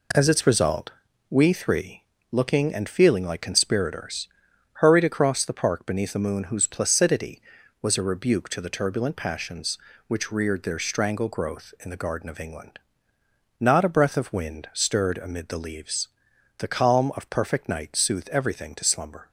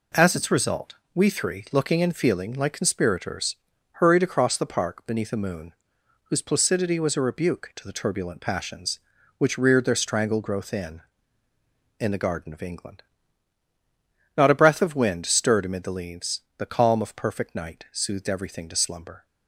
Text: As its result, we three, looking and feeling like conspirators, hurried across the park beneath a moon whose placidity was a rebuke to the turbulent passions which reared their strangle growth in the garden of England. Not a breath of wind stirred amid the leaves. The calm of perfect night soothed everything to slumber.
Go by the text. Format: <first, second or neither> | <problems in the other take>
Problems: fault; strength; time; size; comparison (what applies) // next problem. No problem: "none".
first | pauses between "moon" and "whose"; noticeable; at 5.7 s; 0.52 s long // says "in" twice; at 11.9 s